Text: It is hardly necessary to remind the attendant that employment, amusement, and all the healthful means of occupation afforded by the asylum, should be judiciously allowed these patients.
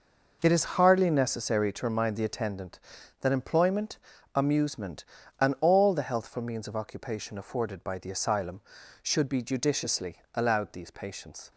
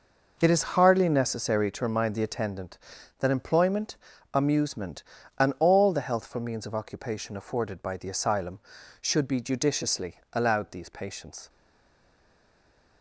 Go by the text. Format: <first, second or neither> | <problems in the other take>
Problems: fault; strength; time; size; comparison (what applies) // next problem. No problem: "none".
first | stays silent after the last word; noticeable; from 11.4 s on; 1.6 s long